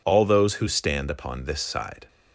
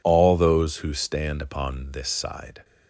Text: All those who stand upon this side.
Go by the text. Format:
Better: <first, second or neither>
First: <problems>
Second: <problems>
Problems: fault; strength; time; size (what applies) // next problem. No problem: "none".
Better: neither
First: none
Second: none